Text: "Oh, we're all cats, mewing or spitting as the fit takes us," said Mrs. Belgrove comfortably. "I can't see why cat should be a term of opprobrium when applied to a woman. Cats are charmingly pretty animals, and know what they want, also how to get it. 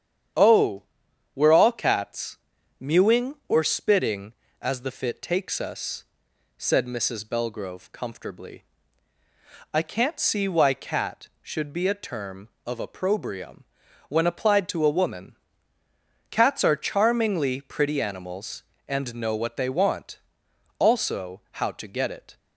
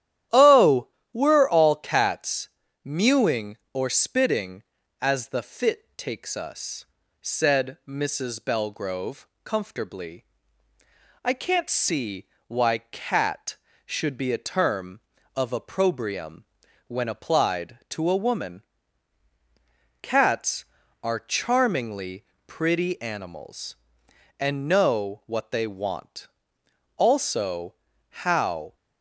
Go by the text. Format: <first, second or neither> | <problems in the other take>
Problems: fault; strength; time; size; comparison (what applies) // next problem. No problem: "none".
first | starts louder than the rest; strong; until 1.5 s; 11.5 dB; strong in the first // pauses between "Belgrove" and "comfortably"; slight; at 9.2 s; 0.16 s long // pauses between "see" and "why"; slight; at 12.2 s; 0.20 s long // pauses between "opprobrium" and "when"; at 16.4 s; 0.44 s long; also in the first // pauses between "charmingly" and "pretty"; slight; at 22.2 s; 0.20 s long // pauses between "also" and "how"; slight; at 27.7 s; 0.34 s long // stops before "to get it"; at 28.7 s